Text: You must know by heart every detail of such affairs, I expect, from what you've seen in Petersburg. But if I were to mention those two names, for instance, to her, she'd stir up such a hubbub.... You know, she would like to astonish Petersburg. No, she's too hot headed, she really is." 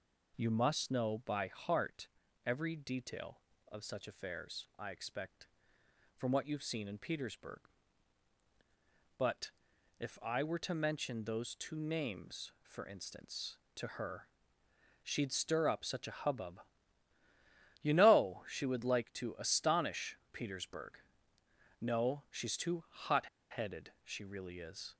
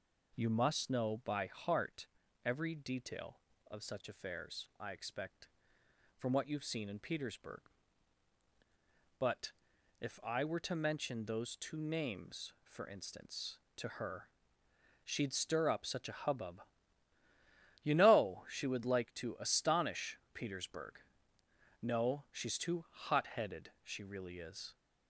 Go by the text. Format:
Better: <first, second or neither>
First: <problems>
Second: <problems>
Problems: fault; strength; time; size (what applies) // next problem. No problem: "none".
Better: second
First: pauses between "heart" and "every"; slight; at 2.0 s; 0.36 s long // pauses between "But" and "if"; noticeable; at 9.5 s; 0.46 s long // pauses between "astonish" and "Petersburg"; slight; at 20.1 s; 0.16 s long // pauses between "hot" and "headed"; slight; at 23.2 s; 0.29 s long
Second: pauses between "heart" and "every"; slight; at 2.0 s; 0.36 s long // pauses between "But" and "if"; noticeable; at 9.5 s; 0.46 s long // pauses between "astonish" and "Petersburg"; slight; at 20.1 s; 0.16 s long